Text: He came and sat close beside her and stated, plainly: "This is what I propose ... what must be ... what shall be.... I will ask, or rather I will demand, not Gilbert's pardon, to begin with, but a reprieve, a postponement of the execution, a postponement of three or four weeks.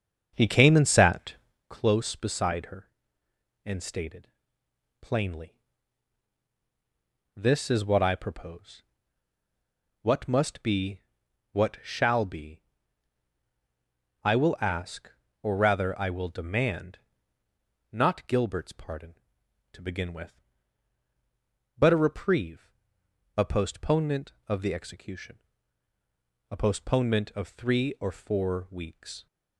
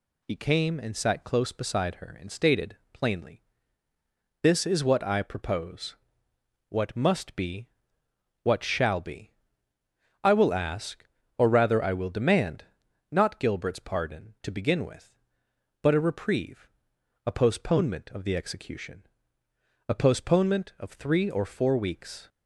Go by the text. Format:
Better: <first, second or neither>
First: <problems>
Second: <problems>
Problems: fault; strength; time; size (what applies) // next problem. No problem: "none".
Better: second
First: starts louder than the rest; until 1.6 s; 6.5 dB // pauses between "sat" and "close"; slight; at 1.3 s; 0.34 s long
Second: none